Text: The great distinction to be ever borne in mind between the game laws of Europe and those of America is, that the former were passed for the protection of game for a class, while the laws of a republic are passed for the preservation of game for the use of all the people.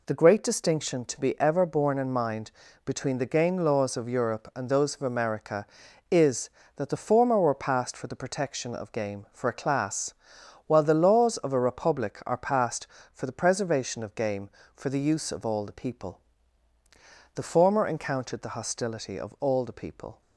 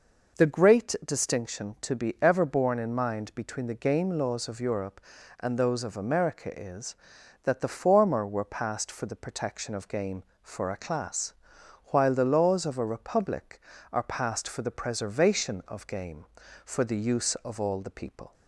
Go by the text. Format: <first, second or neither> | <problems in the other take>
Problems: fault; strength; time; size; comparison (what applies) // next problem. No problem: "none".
second | pauses between "mind" and "between"; slight; at 2.5 s; 0.34 s long // goes on to say "The former encountered the hostility of all the people"; strong; from 17.3 s on; 2.8 s long